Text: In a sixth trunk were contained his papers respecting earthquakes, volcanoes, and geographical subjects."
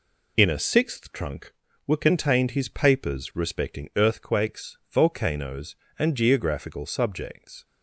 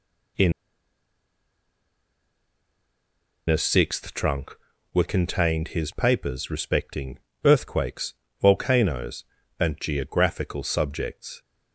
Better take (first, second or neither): first